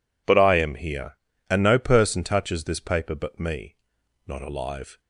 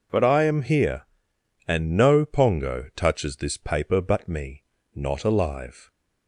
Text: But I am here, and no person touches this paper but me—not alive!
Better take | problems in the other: first | says "pongo" for "person"; at 2.2 s

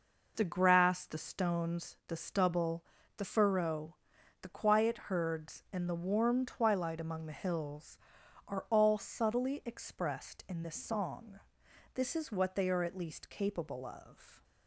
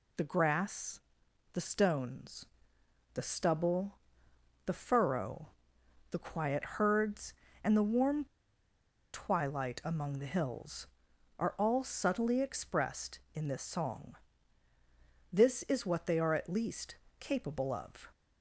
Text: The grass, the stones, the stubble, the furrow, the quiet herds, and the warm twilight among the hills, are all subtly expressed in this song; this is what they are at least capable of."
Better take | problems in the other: first | pauses between "warm" and "twilight"; noticeable; at 8.2 s; 0.88 s long // pauses between "least" and "capable"; slight; at 16.9 s; 0.24 s long

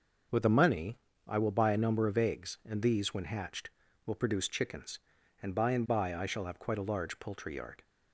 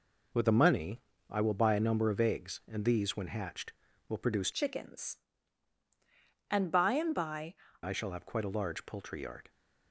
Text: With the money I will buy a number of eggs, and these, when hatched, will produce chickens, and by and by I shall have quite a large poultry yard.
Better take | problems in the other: first | pauses between "money" and "I"; slight; at 1.0 s; 0.28 s long; slight in the first // changes voice from "chickens" to "by"; from 4.5 to 7.5 s; 3.0 s long

